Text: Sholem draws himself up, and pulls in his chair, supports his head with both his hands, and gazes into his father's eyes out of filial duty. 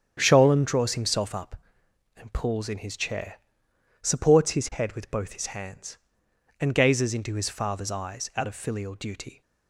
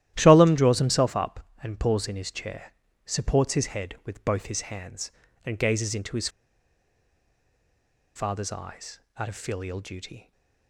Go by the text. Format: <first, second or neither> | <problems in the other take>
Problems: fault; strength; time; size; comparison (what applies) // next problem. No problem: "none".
first | starts louder than the rest; strong; until 1.1 s; 13 dB; strong in the first // pauses between "his" and "father's"; strong; at 6.2 s; 1.8 s long // pauses between "eyes" and "out"; slight; at 8.9 s; 0.18 s long // stays silent after the last word; slight; from 10.1 s on; 0.5 s long